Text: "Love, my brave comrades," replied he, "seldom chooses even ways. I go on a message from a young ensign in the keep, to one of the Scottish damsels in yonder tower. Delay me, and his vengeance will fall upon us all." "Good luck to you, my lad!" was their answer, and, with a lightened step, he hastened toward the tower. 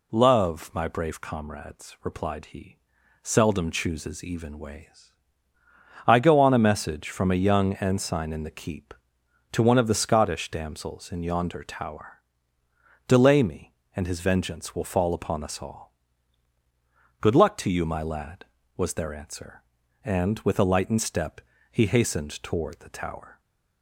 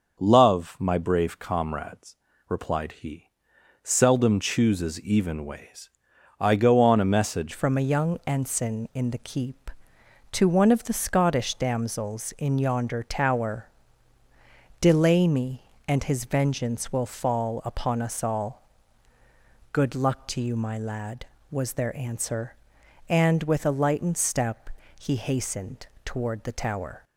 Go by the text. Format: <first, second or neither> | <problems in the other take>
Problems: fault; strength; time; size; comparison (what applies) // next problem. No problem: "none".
first | starts louder than the rest; until 1.2 s; 6 dB // changes voice at "from"; from 7.5 s on; 19.5 s long // pauses between "hastened" and "toward"; slight; at 25.8 s; 0.18 s long